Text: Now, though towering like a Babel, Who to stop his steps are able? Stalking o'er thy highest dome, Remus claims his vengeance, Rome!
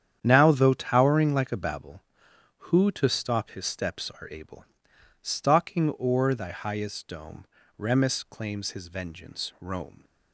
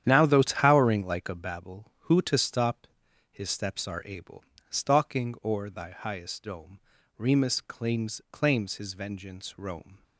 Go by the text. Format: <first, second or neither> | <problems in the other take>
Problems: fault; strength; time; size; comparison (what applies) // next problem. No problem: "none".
first | starts louder than the rest; strong; until 1.0 s; 10 dB; strong in the first // pauses between "stop" and "his"; at 2.8 s; 0.44 s long // says "claims" twice; at 8.3 s